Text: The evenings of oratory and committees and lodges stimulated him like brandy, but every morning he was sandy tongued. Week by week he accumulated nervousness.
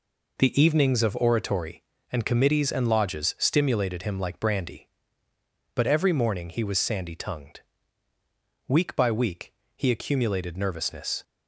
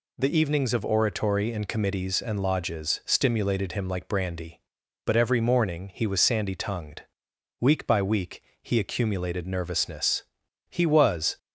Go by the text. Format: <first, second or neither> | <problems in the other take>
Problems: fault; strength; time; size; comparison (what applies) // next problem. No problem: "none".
first | pauses between "week" and "he"; slight; at 8.3 s; 0.22 s long; slight in the first // goes on to say "He was"; noticeable; from 10.6 s on; 0.68 s long